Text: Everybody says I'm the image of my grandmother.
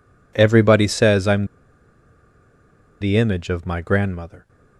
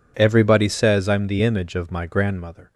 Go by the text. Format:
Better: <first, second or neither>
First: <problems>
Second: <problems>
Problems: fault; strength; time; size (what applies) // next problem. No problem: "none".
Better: second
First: pauses between "I'm" and "the"; strong; at 1.4 s; 1.5 s long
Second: none